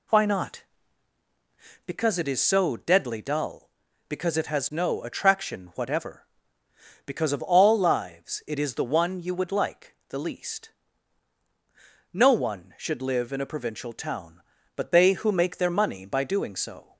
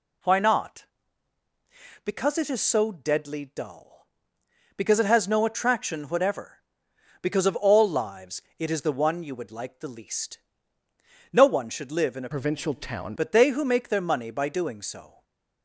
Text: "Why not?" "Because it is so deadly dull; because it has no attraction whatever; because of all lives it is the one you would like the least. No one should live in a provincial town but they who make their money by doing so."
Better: first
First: none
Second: pauses between "lives" and "it"; slight; at 8.4 s; 0.16 s long // changes voice from "provincial" to "town"; from 12.3 to 13.1 s; 0.8 s long // stays silent after the last word; slight; from 15.0 s on; 0.6 s long

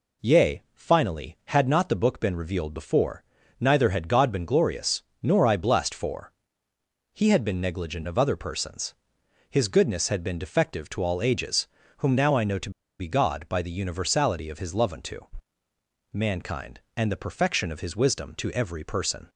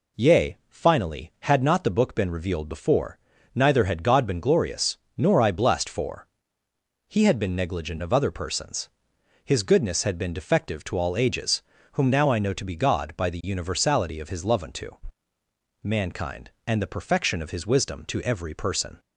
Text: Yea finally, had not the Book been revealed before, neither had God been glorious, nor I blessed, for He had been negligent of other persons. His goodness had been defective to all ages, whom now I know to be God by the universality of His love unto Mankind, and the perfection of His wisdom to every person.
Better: second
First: pauses between "for" and "He"; noticeable; at 6.3 s; 0.84 s long // pauses between "to" and "be"; slight; at 12.7 s; 0.29 s long // pauses between "unto" and "Mankind"; noticeable; at 15.1 s; 0.94 s long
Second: pauses between "for" and "He"; noticeable; at 6.2 s; 0.84 s long // pauses between "unto" and "Mankind"; noticeable; at 14.8 s; 0.94 s long

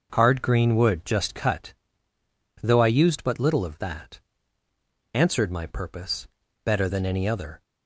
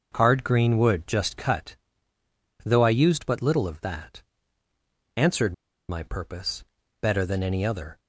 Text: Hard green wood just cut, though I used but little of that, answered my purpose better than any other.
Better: first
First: pauses between "purpose" and "better"; at 6.2 s; 0.38 s long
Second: starts louder than the rest; noticeable; until 1.1 s; 6 dB // pauses between "answered" and "my"; slight; at 5.5 s; 0.34 s long // pauses between "purpose" and "better"; at 6.6 s; 0.38 s long

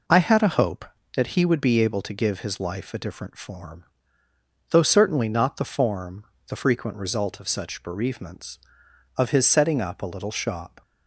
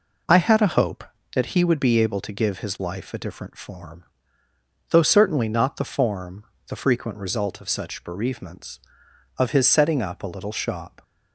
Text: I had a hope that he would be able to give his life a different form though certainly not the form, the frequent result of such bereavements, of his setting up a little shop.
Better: neither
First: pauses between "form" and "though"; noticeable; at 3.8 s; 0.88 s long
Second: pauses between "form" and "though"; noticeable; at 4.0 s; 0.88 s long

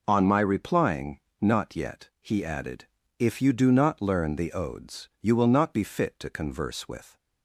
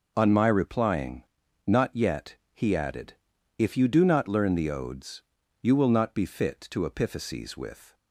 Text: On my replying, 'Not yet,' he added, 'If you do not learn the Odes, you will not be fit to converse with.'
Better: first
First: none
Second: says "epiphyses" for "converse"; at 6.8 s

